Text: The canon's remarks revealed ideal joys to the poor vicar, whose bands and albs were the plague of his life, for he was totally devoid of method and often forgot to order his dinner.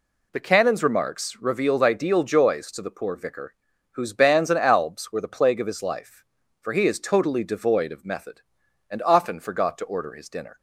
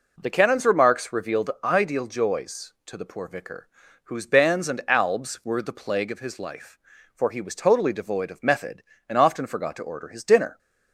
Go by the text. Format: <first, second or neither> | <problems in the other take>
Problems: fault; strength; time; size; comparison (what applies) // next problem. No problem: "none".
second | says "is" for "was"; at 6.8 s